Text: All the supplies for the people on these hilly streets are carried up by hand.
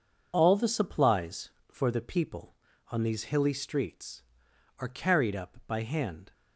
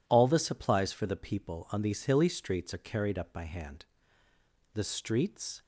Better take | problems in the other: first | goes on to say "The streets"; noticeable; from 4.7 s on; 0.88 s long

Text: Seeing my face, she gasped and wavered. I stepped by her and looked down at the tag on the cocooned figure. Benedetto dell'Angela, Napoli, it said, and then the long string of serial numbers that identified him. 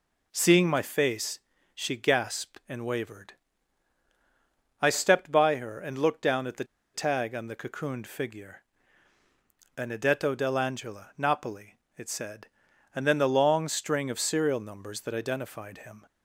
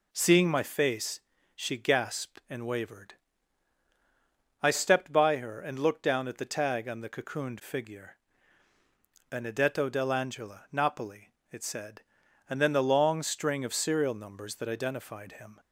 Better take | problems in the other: second | pauses between "the" and "tag"; slight; at 6.6 s; 0.30 s long

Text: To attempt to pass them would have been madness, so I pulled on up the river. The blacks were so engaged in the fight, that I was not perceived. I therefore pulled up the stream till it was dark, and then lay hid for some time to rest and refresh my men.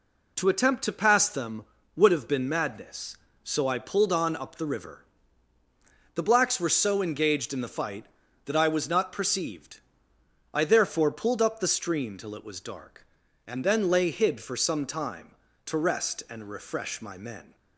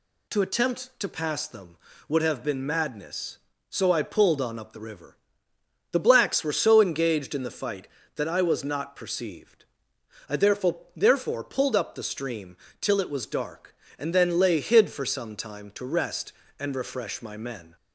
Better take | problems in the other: first | says "therefore" twice; at 10.9 s // pauses between "stream" and "till"; slight; at 12.5 s; 0.24 s long

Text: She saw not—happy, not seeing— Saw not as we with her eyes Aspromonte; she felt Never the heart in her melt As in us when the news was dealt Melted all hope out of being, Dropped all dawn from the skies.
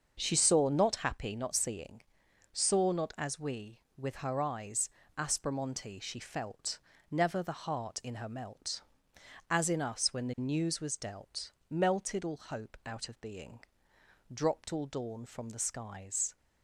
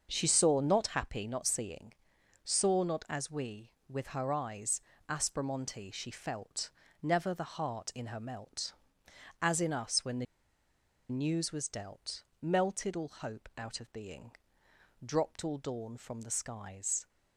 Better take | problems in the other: first | starts louder than the rest; until 1.1 s; 6.5 dB; also in the first // pauses between "eyes" and "Aspromonte"; slight; at 4.7 s; 0.28 s long; slight in the first // pauses between "felt" and "Never"; slight; at 6.7 s; 0.28 s long; slight in the first // pauses between "the" and "news"; noticeable; at 10.2 s; 0.84 s long // pauses between "dealt" and "Melted"; slight; at 12.2 s; 0.18 s long; slight in the first

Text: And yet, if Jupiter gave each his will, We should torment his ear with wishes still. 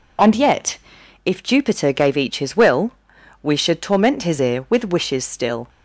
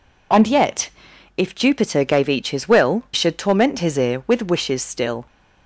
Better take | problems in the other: first | skips "We"; at 3.0 s

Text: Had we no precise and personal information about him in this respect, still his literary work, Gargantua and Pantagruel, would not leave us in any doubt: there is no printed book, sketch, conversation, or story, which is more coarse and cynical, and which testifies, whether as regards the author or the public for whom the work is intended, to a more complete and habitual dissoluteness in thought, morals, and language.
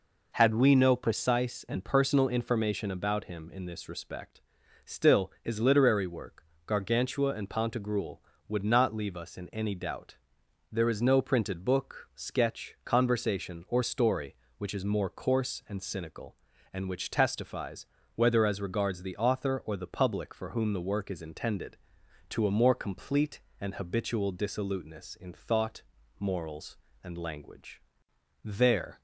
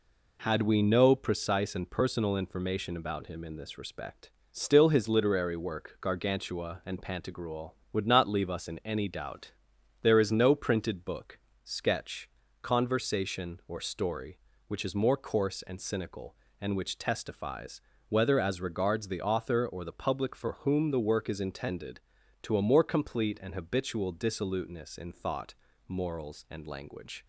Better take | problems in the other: second | goes on to say "There"; from 28.4 s on; 0.56 s long

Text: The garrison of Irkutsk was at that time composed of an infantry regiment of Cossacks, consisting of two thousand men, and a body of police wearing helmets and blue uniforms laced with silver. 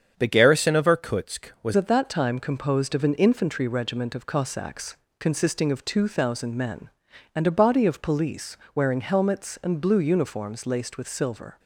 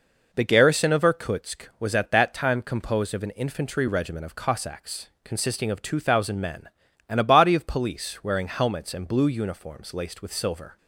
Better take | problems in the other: second | starts louder than the rest; strong; until 1.1 s; 7.5 dB // changes voice at "at"; from 1.7 s on; 9.8 s long // pauses between "police" and "wearing"; slight; at 8.5 s; 0.20 s long

